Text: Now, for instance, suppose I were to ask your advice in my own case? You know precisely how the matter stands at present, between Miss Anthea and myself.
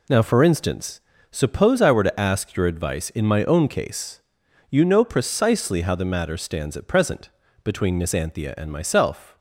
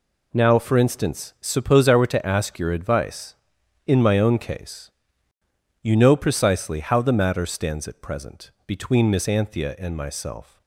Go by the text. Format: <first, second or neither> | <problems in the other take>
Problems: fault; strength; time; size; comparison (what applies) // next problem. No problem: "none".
neither | none